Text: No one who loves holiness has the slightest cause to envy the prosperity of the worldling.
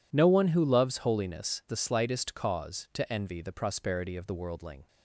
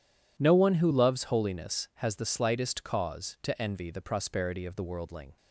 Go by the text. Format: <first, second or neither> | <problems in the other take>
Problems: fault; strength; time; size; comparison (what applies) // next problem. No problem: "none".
second | skips "has"; at 1.6 s